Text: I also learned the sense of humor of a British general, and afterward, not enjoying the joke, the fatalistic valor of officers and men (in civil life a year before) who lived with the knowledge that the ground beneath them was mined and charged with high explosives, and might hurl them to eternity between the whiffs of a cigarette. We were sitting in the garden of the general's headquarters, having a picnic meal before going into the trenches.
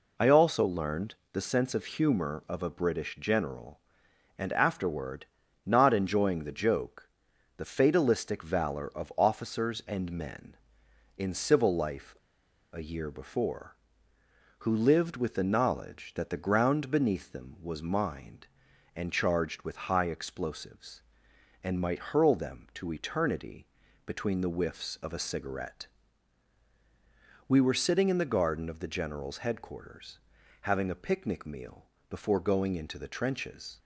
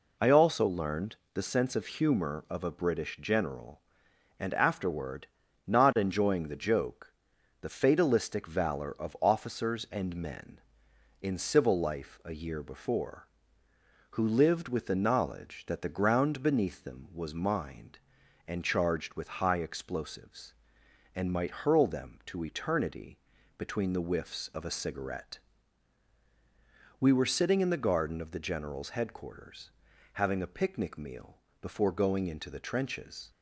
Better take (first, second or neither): second